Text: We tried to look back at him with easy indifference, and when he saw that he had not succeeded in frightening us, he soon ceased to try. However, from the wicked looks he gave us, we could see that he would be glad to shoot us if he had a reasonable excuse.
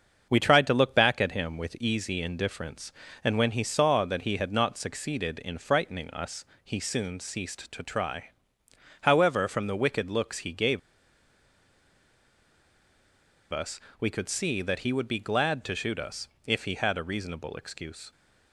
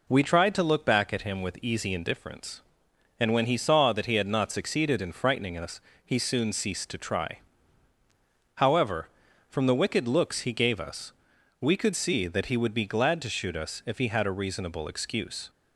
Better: second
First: starts louder than the rest; until 1.3 s; 6.5 dB // pauses between "gave" and "us"; strong; at 10.7 s; 2.7 s long // pauses between "us" and "if"; slight; at 16.2 s; 0.16 s long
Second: none

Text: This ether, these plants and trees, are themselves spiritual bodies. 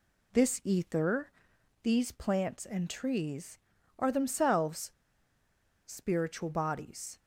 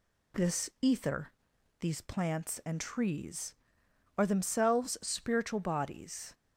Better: second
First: pauses between "themselves" and "spiritual"; noticeable; at 4.9 s; 0.94 s long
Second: none

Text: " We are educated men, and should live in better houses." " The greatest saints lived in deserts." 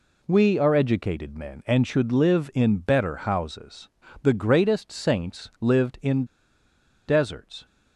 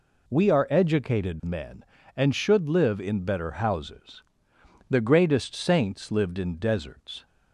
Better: second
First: pauses between "in" and "deserts"; noticeable; at 6.2 s; 0.83 s long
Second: none

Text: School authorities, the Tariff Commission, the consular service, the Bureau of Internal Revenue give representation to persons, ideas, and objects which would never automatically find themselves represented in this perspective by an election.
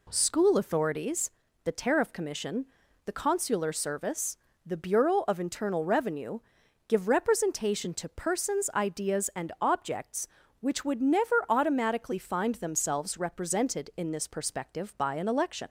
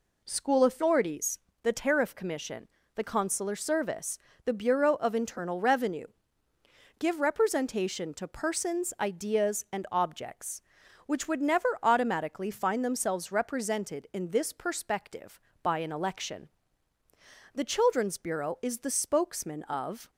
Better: first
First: pauses between "Revenue" and "give"; noticeable; at 6.3 s; 0.50 s long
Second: pauses between "Revenue" and "give"; noticeable; at 6.0 s; 0.92 s long // pauses between "never" and "automatically"; slight; at 11.6 s; 0.16 s long // goes on to say "The Children's Bureau is the spokesman of"; strong; from 17.5 s on; 2.5 s long

